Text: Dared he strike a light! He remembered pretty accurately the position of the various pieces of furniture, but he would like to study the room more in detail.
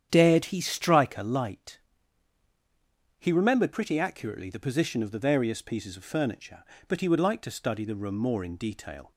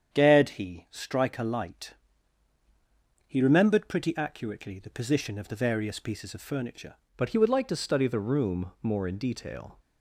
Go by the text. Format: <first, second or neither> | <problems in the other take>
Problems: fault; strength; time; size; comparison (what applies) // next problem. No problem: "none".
first | starts louder than the rest; strong; until 1.2 s; 8.5 dB; strong in the first // changes voice at "but"; from 7.1 s on; 2.6 s long